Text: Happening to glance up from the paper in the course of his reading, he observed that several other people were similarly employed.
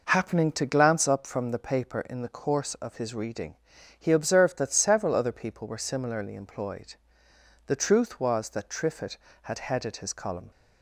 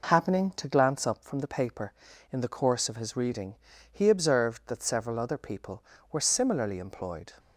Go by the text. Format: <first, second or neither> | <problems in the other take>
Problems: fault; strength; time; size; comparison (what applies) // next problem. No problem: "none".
second | goes on to say "The truth was that Triffitt had headed his column"; strong; from 7.6 s on; 2.8 s long